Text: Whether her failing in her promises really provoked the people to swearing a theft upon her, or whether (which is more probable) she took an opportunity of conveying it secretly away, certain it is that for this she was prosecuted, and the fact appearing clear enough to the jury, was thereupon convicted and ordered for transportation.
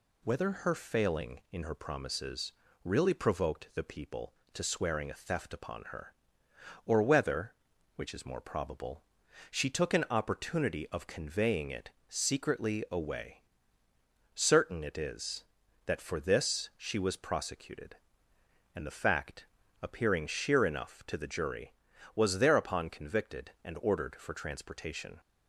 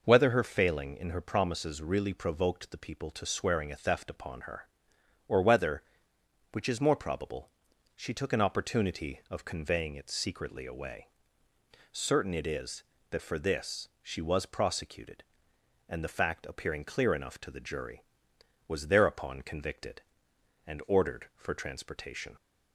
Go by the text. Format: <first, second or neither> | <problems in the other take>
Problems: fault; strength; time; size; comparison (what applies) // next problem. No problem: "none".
second | pauses between "promises" and "really"; slight; at 2.5 s; 0.32 s long // pauses between "it" and "secretly"; slight; at 11.9 s; 0.18 s long // pauses between "fact" and "appearing"; slight; at 19.4 s; 0.36 s long // says "sheer" for "clear"; at 20.2 s